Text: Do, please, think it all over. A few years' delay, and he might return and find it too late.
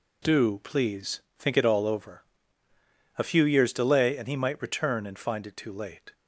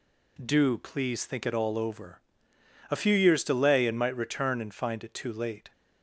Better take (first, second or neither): first